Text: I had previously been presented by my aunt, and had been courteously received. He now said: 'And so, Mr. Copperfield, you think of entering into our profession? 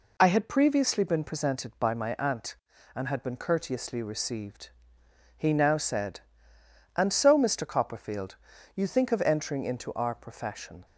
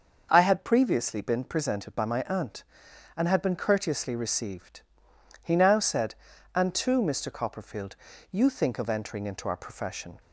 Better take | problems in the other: first | starts louder than the rest; until 1.3 s; 6.5 dB // says "too" for "so"; at 6.7 s

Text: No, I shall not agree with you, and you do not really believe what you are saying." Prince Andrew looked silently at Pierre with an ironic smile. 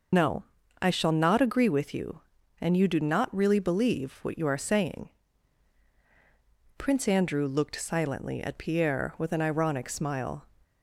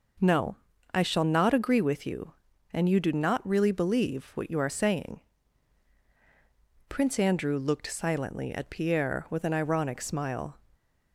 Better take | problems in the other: second | loses the start of "No"; at 0.1 s; 75 ms

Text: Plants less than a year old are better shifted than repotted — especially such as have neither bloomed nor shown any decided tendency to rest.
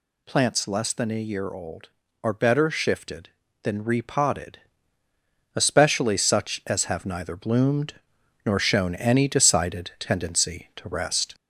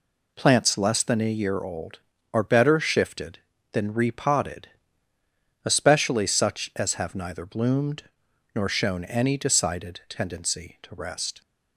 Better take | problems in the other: second | gets louder; slight; throughout; 2.5 dB // pauses between "bloomed" and "nor"; noticeable; at 7.9 s; 0.50 s long; noticeable in the second

